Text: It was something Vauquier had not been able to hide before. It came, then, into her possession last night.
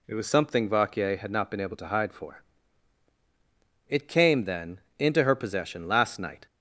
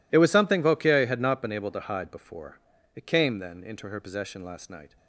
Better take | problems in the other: second | says "for" for "before"; at 2.1 s

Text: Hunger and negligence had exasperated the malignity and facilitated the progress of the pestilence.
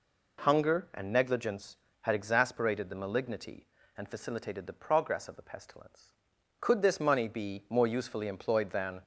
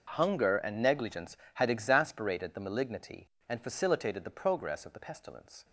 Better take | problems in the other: second | goes on to say "Could this money be more usefully employed than"; strong; from 6.6 s on; 2.4 s long

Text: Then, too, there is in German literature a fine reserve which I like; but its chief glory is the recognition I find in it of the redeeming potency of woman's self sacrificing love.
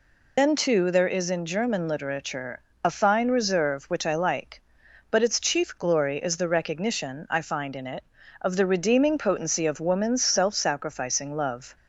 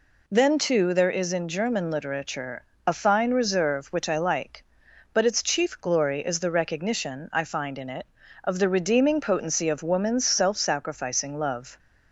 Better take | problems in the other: second | loses the start of "Then"; at 0.3 s; 120 ms // pauses between "literature" and "a"; slight; at 2.6 s; 0.20 s long; slight in the second

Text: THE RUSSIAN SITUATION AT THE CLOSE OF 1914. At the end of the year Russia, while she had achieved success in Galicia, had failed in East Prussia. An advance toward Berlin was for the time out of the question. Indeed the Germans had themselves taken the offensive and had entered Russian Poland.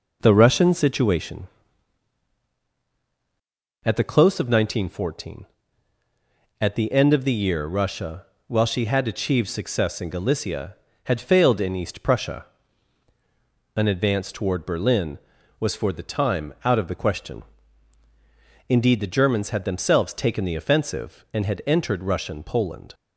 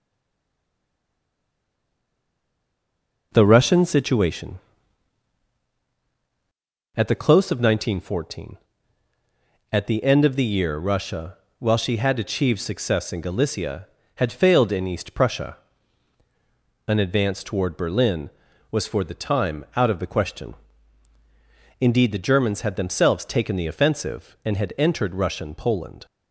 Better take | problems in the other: first | stays silent before the first word; strong; until 3.3 s; 3.3 s long

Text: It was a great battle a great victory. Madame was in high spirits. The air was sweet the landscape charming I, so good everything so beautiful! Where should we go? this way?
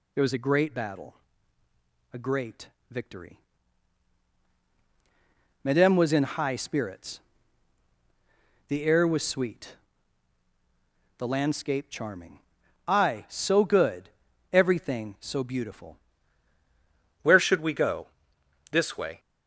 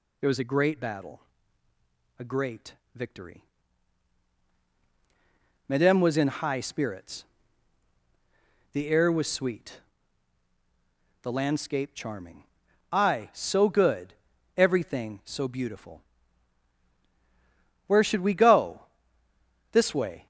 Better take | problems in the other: second | pauses between "battle" and "a"; at 1.1 s; 1.0 s long; also in the second // pauses between "great" and "victory"; slight; at 2.6 s; 0.22 s long; slight in the second // pauses between "sweet" and "the"; strong; at 9.7 s; 1.4 s long; strong in the second // pauses between "charming" and "I"; noticeable; at 12.3 s; 0.46 s long; noticeable in the second // pauses between "good" and "everything"; at 14.0 s; 0.42 s long; also in the second // changes voice at "Where"; from 17.2 s on; 1.9 s long

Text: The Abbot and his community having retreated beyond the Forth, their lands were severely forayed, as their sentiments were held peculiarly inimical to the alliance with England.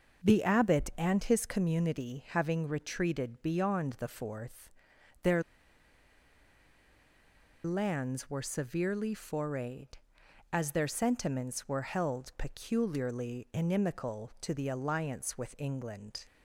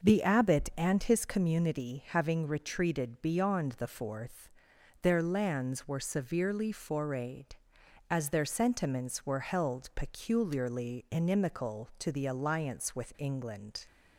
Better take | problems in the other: second | pauses between "their" and "lands"; strong; at 5.4 s; 2.2 s long

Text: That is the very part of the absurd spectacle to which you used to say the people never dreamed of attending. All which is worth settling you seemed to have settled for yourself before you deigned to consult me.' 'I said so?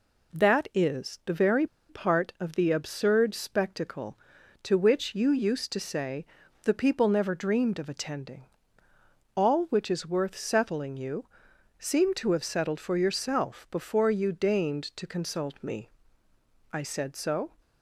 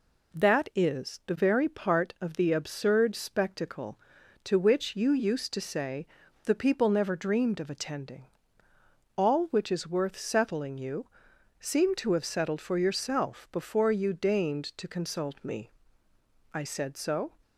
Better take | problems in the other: second | pauses between "very" and "part"; slight; at 1.6 s; 0.22 s long // pauses between "say" and "the"; at 6.2 s; 0.38 s long; also in the second // pauses between "you" and "seemed"; noticeable; at 11.2 s; 0.52 s long; noticeable in the second

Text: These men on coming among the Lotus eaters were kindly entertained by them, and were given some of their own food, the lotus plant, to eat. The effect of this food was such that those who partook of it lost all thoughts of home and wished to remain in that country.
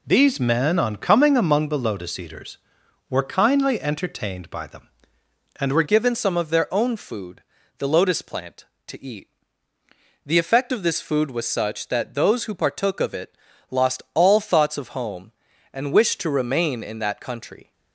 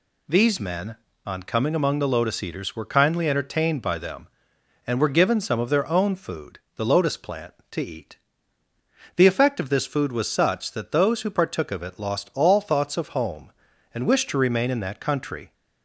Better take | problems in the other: second | changes voice at "given"; from 5.8 s on; 11.9 s long // pauses between "it" and "lost"; slight; at 13.3 s; 0.34 s long

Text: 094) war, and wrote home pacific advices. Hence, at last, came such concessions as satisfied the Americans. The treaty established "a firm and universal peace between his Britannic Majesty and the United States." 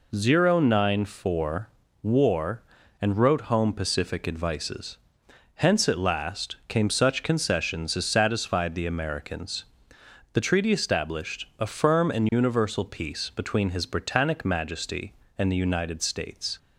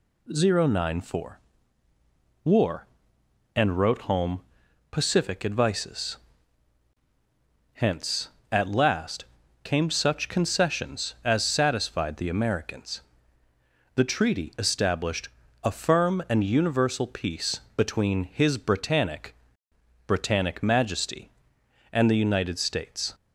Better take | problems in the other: first | pauses between "home" and "pacific"; noticeable; at 4.4 s; 0.50 s long // pauses between "established" and "a"; slight; at 15.2 s; 0.34 s long // pauses between "peace" and "between"; slight; at 17.6 s; 0.16 s long // says "Britannic" twice; at 20.0 s

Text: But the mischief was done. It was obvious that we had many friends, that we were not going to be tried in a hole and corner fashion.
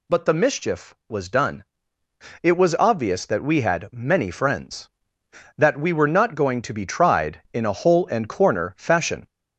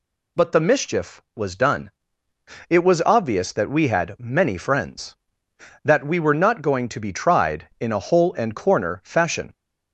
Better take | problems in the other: second | gets louder; slight; throughout; 2.5 dB

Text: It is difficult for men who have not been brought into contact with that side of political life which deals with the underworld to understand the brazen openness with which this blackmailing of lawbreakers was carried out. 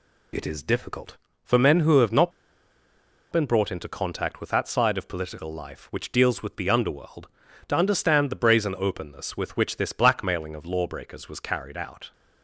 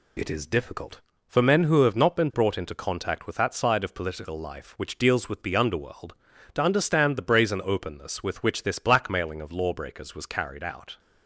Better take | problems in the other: second | pauses between "not" and "been"; at 2.3 s; 1.0 s long

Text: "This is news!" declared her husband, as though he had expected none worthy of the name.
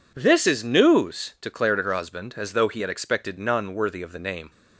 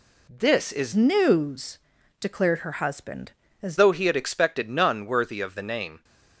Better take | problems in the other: first | changes voice from "news" to "as"; from 0.9 to 3.7 s; 2.8 s long

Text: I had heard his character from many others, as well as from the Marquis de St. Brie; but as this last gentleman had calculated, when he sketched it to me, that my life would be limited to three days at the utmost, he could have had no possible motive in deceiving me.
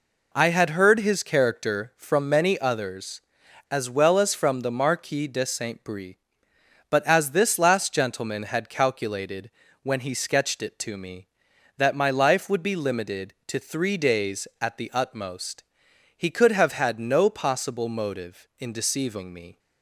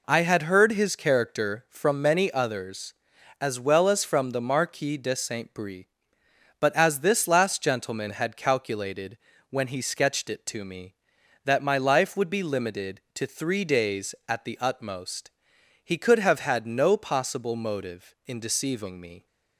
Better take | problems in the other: neither | none

